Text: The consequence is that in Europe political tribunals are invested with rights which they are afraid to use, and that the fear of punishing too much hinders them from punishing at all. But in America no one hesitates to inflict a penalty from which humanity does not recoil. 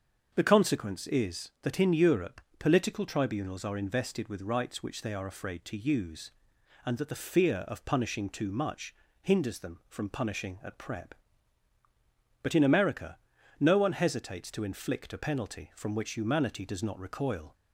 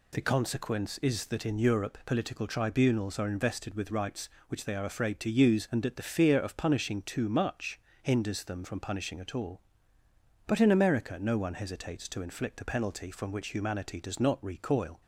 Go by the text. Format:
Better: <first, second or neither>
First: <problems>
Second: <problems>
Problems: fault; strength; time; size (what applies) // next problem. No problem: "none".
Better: second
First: starts louder than the rest; until 1.3 s; 6.5 dB // pauses between "Europe" and "political"; slight; at 2.4 s; 0.18 s long // pauses between "much" and "hinders"; slight; at 8.9 s; 0.26 s long // says "prep" for "all"; at 10.7 s // pauses between "America" and "no"; at 13.1 s; 0.42 s long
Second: pauses between "much" and "hinders"; slight; at 7.7 s; 0.20 s long